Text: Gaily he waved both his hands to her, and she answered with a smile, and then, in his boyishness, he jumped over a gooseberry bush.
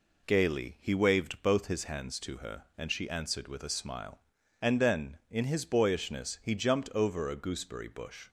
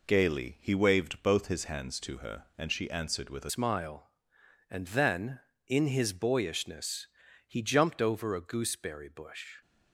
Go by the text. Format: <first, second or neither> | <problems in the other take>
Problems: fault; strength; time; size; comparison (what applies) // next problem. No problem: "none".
first | changes voice at "smile"; from 3.4 s on; 6.1 s long